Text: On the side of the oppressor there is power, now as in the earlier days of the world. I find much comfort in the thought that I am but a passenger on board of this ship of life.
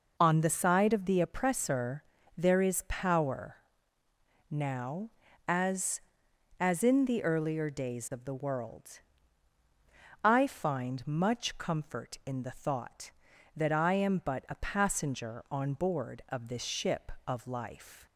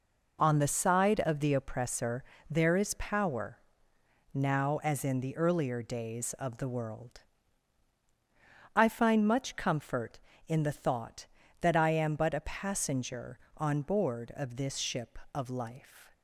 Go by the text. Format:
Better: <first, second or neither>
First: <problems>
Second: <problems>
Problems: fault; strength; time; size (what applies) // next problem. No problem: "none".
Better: second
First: pauses between "oppressor" and "there"; slight; at 2.0 s; 0.32 s long // says "as" twice; at 6.5 s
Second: pauses between "oppressor" and "there"; slight; at 2.2 s; 0.26 s long